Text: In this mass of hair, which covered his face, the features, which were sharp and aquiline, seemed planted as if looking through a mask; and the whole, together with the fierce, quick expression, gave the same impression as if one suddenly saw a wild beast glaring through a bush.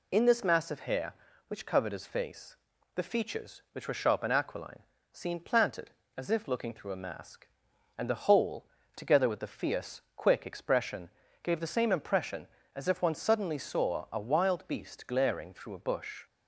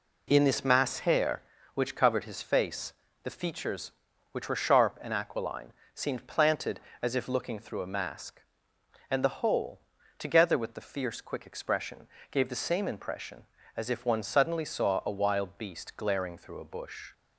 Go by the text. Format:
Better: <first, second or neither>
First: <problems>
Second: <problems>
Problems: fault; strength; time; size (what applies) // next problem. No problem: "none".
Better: first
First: none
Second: skips "of"; at 0.9 s